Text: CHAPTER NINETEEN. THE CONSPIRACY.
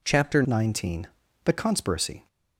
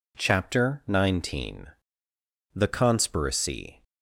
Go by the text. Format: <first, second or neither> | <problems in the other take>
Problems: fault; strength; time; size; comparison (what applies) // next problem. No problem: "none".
second | changes voice at "NINETEEN"; from 0.4 s on; 1.8 s long